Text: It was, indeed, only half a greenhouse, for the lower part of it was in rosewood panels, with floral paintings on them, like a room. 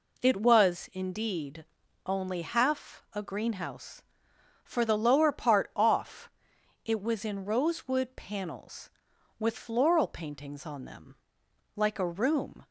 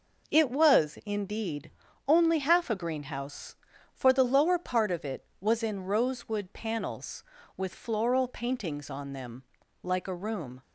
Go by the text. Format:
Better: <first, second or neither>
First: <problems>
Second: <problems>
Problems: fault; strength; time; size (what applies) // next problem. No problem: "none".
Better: second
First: says "off" for "of"; at 5.7 s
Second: none